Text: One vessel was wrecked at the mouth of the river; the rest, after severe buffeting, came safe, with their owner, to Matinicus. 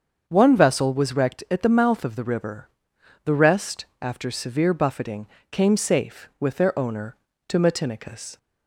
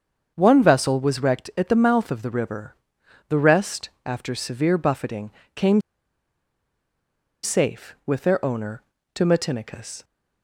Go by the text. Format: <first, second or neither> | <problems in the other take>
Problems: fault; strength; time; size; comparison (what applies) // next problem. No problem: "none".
first | starts louder than the rest; until 1.3 s; 7 dB; also in the first // pauses between "came" and "safe"; strong; at 5.7 s; 1.6 s long